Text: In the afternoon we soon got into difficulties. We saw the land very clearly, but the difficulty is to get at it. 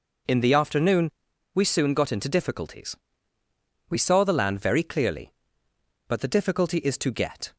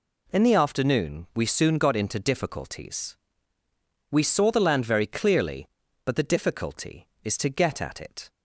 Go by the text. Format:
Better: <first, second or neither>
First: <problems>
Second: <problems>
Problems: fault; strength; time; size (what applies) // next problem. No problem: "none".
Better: second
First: pauses between "afternoon" and "we"; at 1.1 s; 0.42 s long // stops before "at it"; at 7.5 s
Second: none